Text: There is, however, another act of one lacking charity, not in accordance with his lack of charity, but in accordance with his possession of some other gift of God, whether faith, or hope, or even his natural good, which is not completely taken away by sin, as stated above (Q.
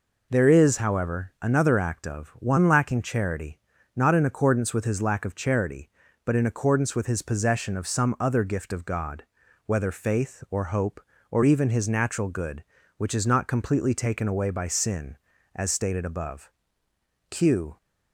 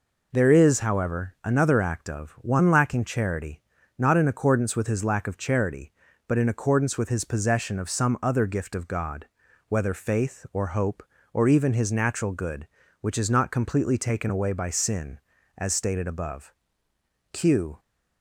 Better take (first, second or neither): neither